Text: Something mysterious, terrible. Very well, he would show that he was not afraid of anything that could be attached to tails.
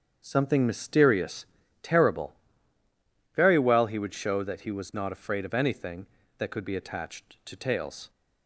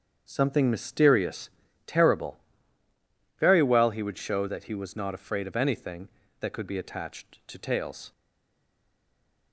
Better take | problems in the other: first | starts louder than the rest; strong; until 1.2 s; 8 dB; strong in the first // stays silent after the last word; noticeable; from 8.1 s on; 1.4 s long

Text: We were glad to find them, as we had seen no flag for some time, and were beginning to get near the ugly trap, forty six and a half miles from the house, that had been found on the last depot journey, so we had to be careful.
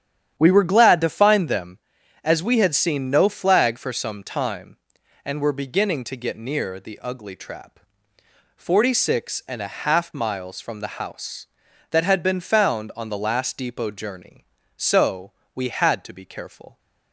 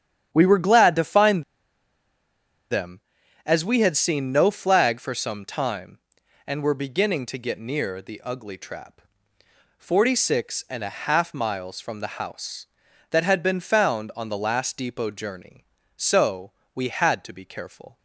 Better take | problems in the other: first | starts louder than the rest; strong; until 1.3 s; 9.5 dB; strong in the first // pauses between "find" and "them"; strong; at 1.4 s; 1.2 s long // pauses between "so" and "we"; slight; at 16.5 s; 0.22 s long; slight in the first

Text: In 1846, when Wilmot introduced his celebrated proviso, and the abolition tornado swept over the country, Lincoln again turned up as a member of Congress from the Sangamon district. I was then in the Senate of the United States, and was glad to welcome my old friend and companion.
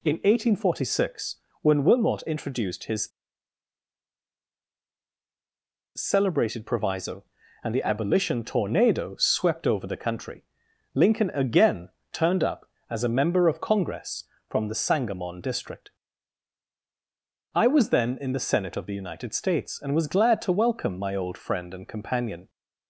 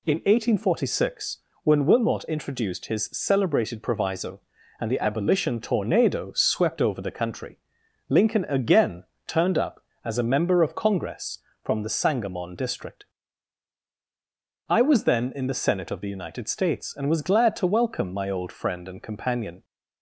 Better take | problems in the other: second | pauses between "his" and "celebrated"; strong; at 3.0 s; 2.8 s long // pauses between "again" and "turned"; slight; at 11.8 s; 0.22 s long; slight in the second

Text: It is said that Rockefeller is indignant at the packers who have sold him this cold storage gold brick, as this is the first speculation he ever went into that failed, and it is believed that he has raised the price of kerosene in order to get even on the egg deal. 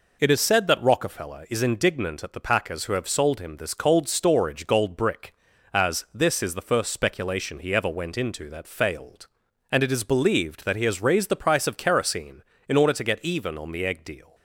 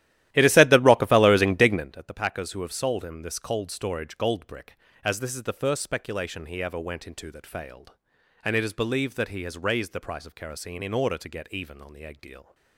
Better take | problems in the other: first | starts louder than the rest; strong; until 1.9 s; 14 dB

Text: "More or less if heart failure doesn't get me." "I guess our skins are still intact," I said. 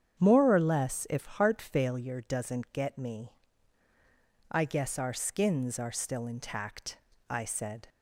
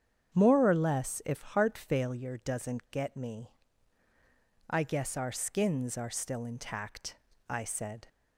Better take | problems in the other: neither | starts louder than the rest; strong; the same in both

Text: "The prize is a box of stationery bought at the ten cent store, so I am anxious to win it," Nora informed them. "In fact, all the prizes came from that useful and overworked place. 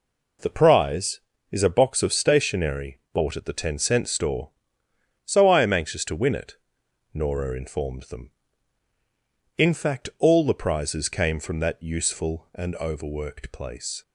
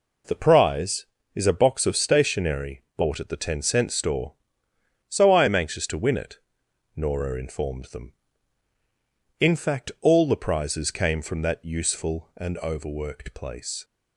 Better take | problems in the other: neither | pauses between "stationery" and "bought"; slight; the same in both

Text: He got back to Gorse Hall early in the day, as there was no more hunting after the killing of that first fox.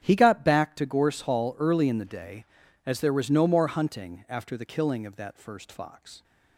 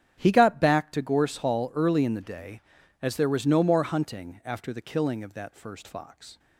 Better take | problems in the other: neither | starts louder than the rest; strong; the same in both

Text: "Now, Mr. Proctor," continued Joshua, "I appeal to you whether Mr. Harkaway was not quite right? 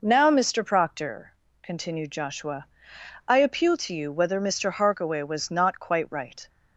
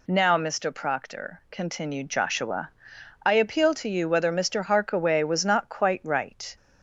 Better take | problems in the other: neither | none

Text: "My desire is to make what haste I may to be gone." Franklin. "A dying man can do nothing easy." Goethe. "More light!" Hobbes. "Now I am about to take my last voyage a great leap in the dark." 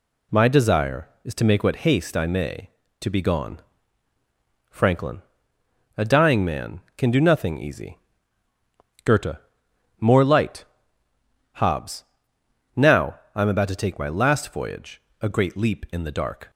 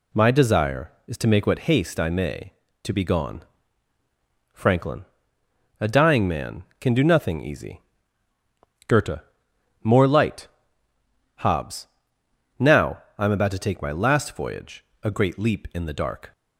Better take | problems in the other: neither | pauses between "Now" and "I"; slight; the same in both // pauses between "voyage" and "a"; slight; the same in both

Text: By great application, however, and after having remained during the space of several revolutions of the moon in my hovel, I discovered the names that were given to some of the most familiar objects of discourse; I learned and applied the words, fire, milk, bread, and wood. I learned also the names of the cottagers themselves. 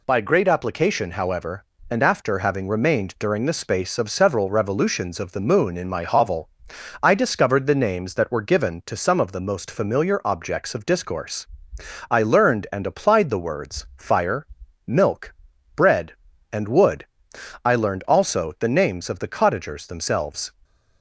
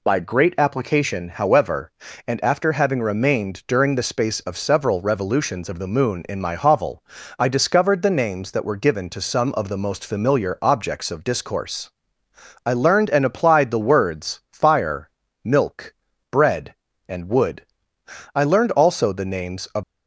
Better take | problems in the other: first | stops before "the cottagers themselves"; at 19.8 s

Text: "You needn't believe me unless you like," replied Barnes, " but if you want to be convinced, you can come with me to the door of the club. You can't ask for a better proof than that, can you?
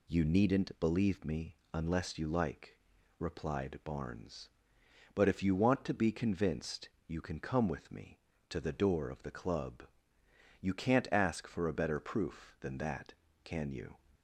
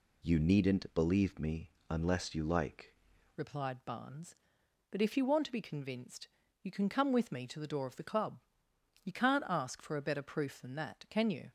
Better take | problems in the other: first | pauses between "me" and "unless"; slight; at 1.7 s; 0.16 s long // changes voice at "replied"; from 3.3 s on; 8.2 s long

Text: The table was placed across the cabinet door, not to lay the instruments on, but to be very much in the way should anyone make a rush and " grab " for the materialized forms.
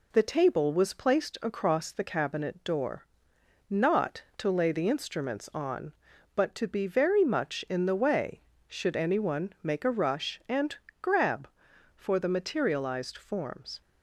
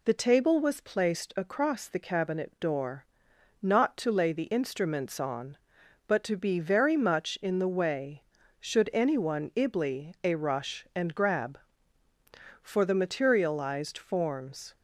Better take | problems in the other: first | says "ibly" for "make"; at 9.5 s

